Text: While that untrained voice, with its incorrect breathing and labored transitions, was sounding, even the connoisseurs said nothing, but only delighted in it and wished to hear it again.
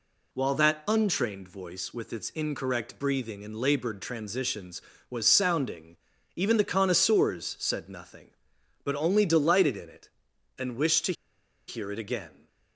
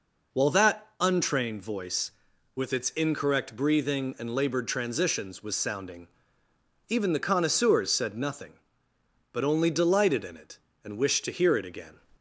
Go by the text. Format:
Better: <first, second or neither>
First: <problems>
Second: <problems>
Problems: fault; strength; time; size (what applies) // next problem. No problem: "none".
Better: second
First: pauses between "to" and "hear"; noticeable; at 11.1 s; 0.55 s long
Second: none